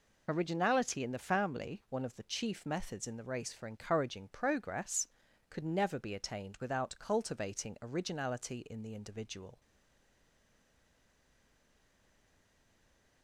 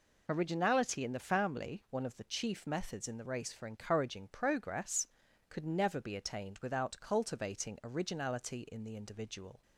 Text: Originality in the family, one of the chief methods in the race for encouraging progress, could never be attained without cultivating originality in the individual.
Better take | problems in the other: second | stays silent after the last word; strong; from 9.6 s on; 3.6 s long

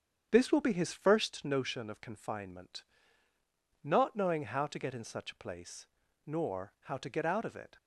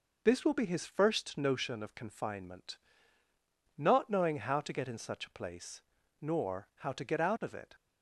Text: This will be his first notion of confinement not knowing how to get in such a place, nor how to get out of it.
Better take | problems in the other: second | starts louder than the rest; strong; until 1.3 s; 8 dB // pauses between "confinement" and "not"; at 2.8 s; 1.0 s long; also in the second

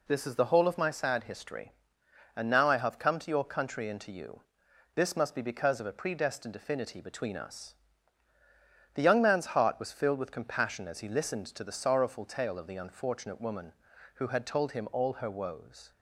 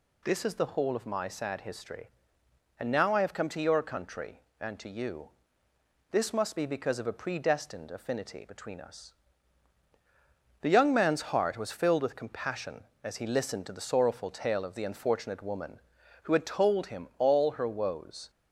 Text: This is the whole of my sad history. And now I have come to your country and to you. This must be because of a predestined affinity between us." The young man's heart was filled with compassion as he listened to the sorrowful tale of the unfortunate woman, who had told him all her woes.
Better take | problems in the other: neither | none

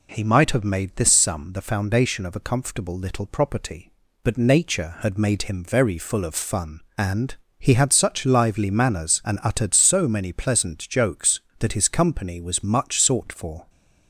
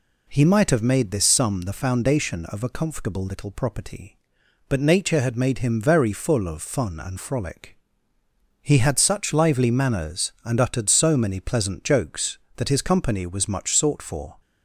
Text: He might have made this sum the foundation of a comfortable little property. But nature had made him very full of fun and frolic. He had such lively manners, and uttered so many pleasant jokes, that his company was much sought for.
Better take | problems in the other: second | skips "frolic"; at 7.4 s

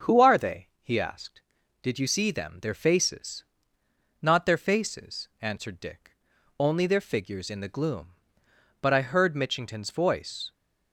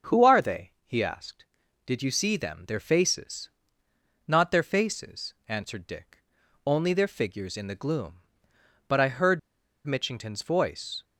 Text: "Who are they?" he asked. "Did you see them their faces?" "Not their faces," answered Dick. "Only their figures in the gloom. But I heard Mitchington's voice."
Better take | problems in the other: first | starts louder than the rest; until 1.2 s; 7 dB; also in the first // pauses between "heard" and "Mitchington's"; noticeable; at 9.3 s; 0.46 s long

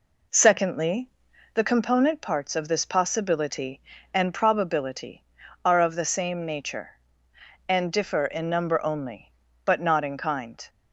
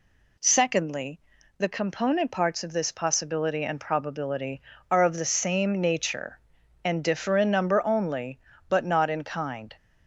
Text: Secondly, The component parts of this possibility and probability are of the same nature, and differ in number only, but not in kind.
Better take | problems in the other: second | starts louder than the rest; until 1.9 s; 4 dB

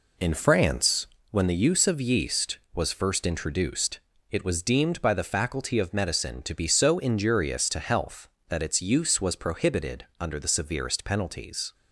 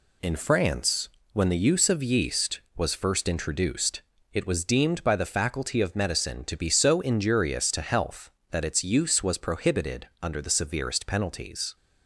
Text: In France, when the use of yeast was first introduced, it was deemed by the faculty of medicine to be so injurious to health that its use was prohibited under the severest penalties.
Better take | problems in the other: second | starts louder than the rest; until 1.3 s; 3.5 dB // pauses between "prohibited" and "under"; slight; at 10.0 s; 0.16 s long; slight in the second

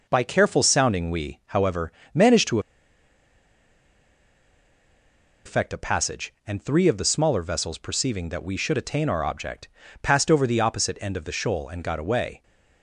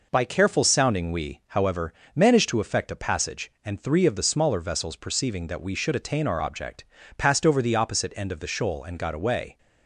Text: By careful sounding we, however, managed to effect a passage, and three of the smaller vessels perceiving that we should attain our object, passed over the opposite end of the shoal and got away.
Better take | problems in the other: second | pauses between "to" and "effect"; strong; at 2.5 s; 2.8 s long

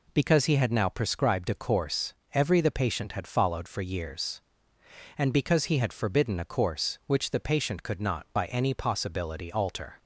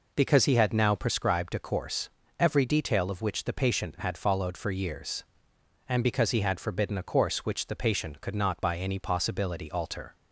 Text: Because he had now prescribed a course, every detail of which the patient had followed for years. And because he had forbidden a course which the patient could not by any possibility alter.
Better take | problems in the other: second | skips "detail of which"; at 2.6 s

